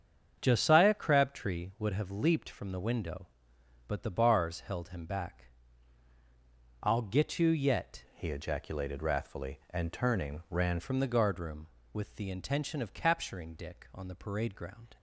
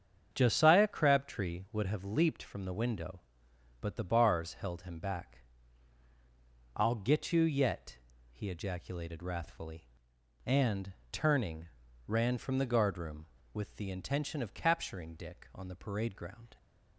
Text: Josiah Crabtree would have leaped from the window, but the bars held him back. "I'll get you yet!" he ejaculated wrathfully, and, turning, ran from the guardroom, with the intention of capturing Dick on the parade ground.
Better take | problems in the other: second | starts louder than the rest; strong; until 1.4 s; 7.5 dB; strong in the second // changes voice from "he" to "ran"; from 8.1 to 10.7 s; 2.6 s long

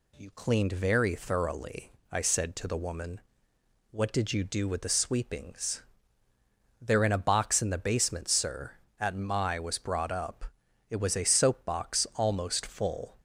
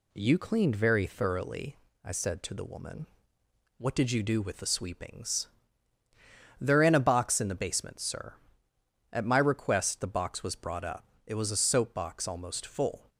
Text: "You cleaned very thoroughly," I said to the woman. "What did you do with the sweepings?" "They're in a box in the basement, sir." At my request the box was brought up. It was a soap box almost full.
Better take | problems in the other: second | skips "request the box"; at 9.5 s

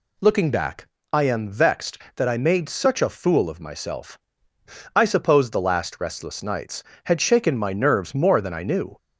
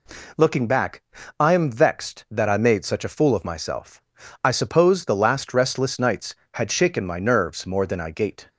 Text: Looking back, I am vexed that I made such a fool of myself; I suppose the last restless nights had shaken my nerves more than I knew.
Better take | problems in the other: first | says "gait" for "knew"; at 8.1 s

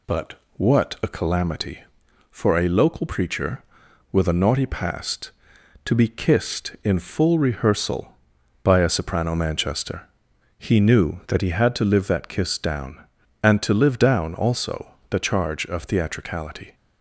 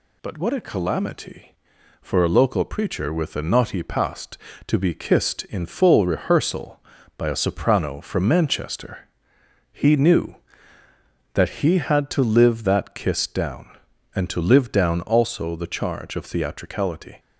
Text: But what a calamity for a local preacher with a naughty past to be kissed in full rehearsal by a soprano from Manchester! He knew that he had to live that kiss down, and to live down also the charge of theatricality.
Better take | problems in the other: second | pauses between "But" and "what"; slight; at 0.3 s; 0.22 s long // skips "from"; at 9.3 s // pauses between "also" and "the"; slight; at 14.9 s; 0.16 s long

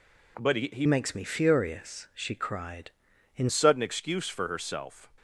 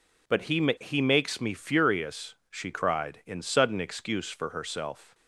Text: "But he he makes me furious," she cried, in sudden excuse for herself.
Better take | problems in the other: second | changes voice from "makes" to "in"; from 0.8 to 3.4 s; 2.6 s long

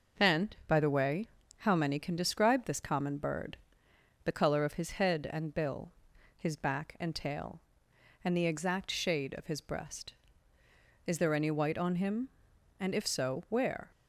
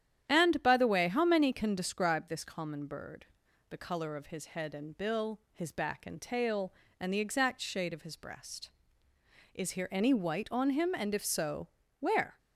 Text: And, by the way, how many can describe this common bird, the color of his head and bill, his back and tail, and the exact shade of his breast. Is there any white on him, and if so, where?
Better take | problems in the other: first | starts louder than the rest; strong; until 1.3 s; 10 dB // says "here" for "there"; at 9.7 s

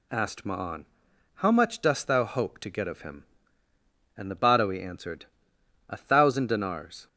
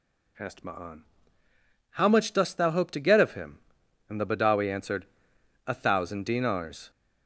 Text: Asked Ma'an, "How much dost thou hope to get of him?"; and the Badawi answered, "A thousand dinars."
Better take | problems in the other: neither | none

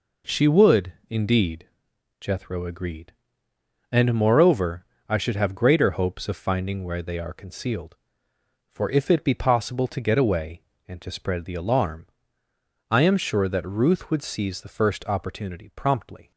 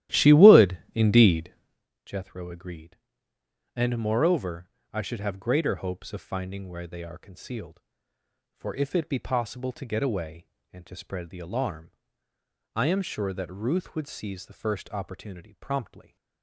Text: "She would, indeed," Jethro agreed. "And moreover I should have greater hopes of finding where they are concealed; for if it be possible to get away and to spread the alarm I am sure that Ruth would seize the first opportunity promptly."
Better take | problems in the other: first | starts louder than the rest; strong; until 1.9 s; 13.5 dB // pauses between "moreover" and "I"; slight; at 4.6 s; 0.24 s long; slight in the first // pauses between "alarm" and "I"; noticeable; at 11.9 s; 0.82 s long; noticeable in the first

